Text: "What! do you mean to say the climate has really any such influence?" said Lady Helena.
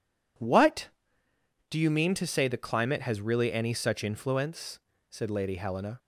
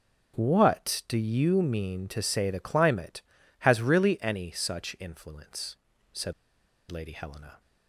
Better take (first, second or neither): first